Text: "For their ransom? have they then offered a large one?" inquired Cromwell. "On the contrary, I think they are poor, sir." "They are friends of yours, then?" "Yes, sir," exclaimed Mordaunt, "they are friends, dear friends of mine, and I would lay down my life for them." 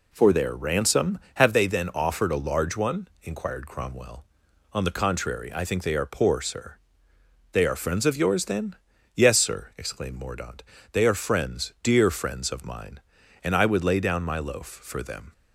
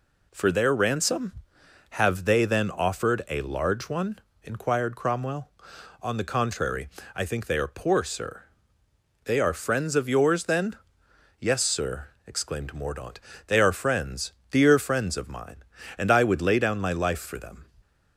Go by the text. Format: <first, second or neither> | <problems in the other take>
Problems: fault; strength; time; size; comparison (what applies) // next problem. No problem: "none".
second | says "loaf" for "life"; at 14.3 s